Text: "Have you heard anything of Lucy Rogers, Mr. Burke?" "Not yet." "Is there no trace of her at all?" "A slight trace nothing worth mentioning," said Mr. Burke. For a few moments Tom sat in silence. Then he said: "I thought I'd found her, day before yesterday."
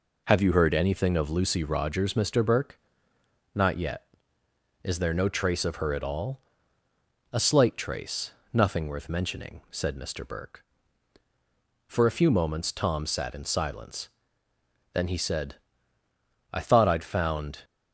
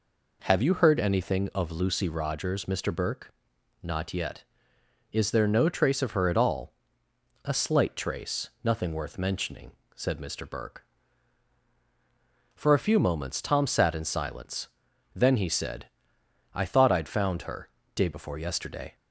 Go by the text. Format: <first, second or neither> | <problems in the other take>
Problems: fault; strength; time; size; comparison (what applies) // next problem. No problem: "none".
second | pauses between "trace" and "nothing"; slight; at 8.3 s; 0.22 s long // stops before "her day before yesterday"; at 17.6 s